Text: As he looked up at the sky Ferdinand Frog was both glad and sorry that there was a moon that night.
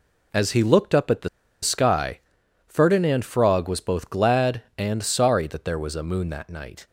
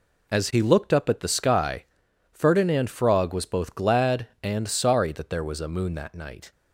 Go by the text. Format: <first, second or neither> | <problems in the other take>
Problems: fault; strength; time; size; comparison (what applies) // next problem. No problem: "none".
second | pauses between "the" and "sky"; slight; at 1.2 s; 0.34 s long // pauses between "sky" and "Ferdinand"; noticeable; at 2.1 s; 0.48 s long; noticeable in the second